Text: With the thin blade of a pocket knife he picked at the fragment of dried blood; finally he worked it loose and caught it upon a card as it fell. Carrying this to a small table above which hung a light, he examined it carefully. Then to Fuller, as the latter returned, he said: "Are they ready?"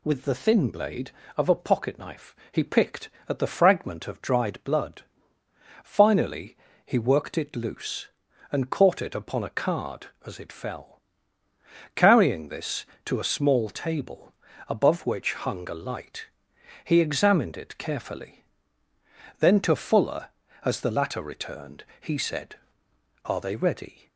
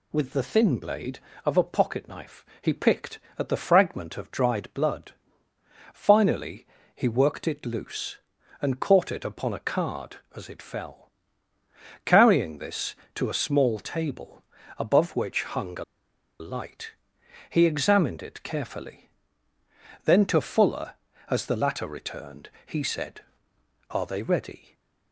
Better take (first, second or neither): first